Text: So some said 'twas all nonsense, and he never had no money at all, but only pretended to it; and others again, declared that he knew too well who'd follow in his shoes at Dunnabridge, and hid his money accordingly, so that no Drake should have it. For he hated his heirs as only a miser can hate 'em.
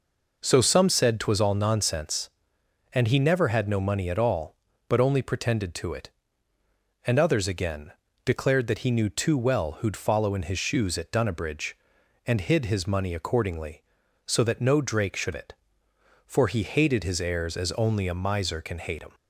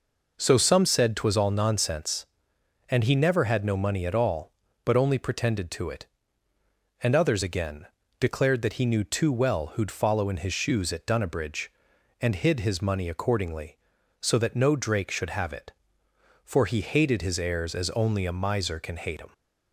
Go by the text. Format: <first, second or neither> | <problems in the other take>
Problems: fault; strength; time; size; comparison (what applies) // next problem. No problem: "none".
second | skips "have"; at 15.3 s